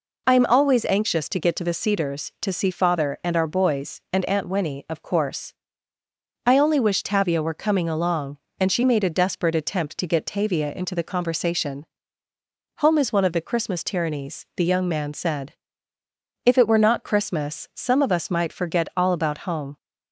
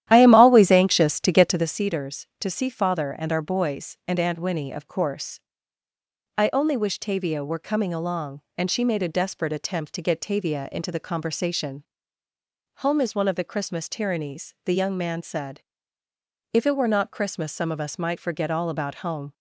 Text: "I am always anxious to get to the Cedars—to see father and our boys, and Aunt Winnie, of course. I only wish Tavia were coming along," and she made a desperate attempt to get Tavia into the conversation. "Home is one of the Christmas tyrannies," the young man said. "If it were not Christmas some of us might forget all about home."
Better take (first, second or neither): first